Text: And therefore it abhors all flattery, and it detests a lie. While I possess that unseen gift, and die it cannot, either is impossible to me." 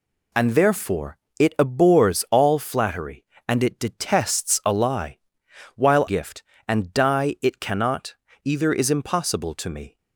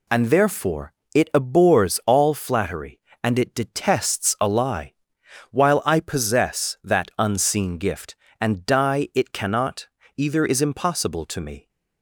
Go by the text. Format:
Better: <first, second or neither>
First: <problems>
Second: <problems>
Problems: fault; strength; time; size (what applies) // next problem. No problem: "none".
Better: second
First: pauses between "therefore" and "it"; slight; at 1.1 s; 0.22 s long // skips "I possess that unseen"; at 6.0 s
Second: pauses between "therefore" and "it"; slight; at 0.9 s; 0.22 s long